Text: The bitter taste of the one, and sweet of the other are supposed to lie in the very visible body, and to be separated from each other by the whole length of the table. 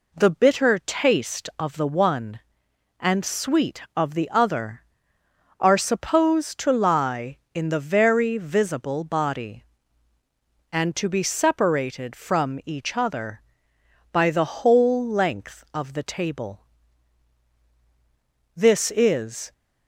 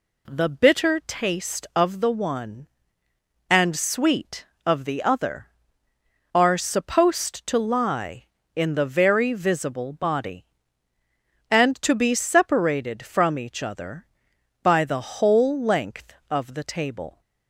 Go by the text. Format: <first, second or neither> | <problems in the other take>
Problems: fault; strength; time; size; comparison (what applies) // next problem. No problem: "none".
second | goes on to say "This is"; noticeable; from 18.5 s on; 0.98 s long